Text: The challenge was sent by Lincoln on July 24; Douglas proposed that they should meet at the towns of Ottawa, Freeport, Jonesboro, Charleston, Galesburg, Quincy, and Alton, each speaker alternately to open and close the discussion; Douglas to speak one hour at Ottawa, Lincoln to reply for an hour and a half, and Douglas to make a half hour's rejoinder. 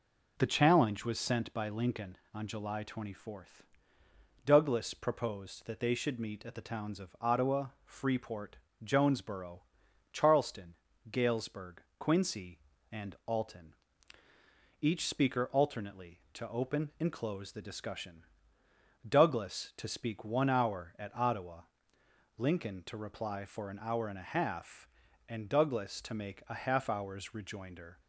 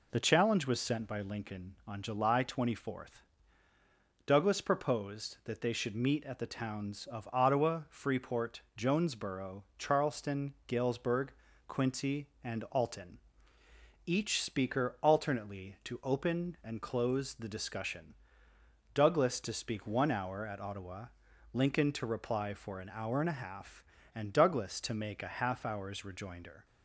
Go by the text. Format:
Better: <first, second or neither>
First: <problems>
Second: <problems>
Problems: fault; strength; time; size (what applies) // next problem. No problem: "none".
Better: neither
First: none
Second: none